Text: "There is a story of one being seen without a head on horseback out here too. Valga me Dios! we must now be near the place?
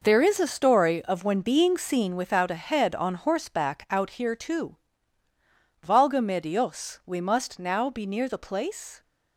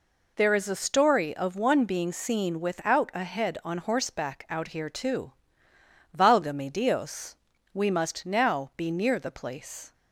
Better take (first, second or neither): second